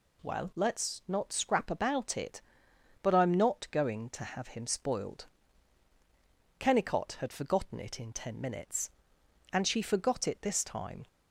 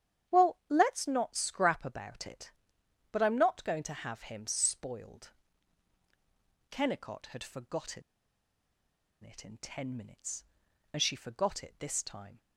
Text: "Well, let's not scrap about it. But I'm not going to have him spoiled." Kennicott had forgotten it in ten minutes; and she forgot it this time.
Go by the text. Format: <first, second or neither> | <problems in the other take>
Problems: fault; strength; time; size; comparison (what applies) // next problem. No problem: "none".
first | starts louder than the rest; strong; until 1.4 s; 10 dB // pauses between "forgotten" and "it"; at 8.0 s; 1.2 s long